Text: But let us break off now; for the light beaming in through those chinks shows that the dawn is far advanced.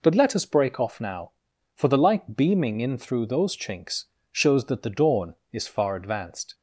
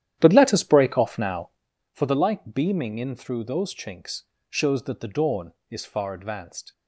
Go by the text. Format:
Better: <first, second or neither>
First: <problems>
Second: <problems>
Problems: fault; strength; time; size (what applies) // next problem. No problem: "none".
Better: first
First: pauses between "chinks" and "shows"; slight; at 4.0 s; 0.26 s long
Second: starts louder than the rest; strong; until 1.7 s; 11 dB // pauses between "chinks" and "shows"; slight; at 4.2 s; 0.26 s long